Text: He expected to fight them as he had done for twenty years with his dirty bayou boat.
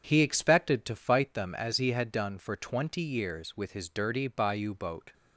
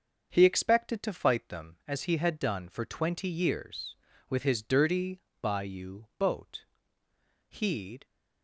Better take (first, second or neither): first